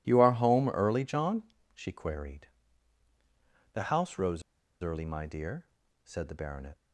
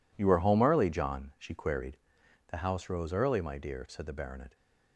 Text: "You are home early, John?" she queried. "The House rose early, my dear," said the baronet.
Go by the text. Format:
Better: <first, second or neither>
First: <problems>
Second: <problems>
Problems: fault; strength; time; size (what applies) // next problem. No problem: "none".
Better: second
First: pauses between "rose" and "early"; at 4.4 s; 0.39 s long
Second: none